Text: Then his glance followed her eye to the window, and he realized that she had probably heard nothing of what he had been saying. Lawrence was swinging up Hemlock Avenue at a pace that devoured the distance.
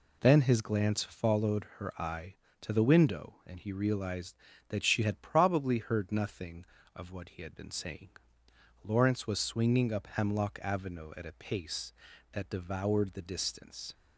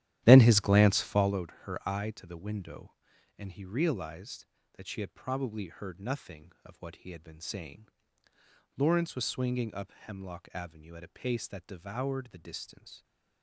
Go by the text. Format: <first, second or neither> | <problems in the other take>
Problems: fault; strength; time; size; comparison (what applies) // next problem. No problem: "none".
first | starts louder than the rest; strong; until 1.4 s; 13 dB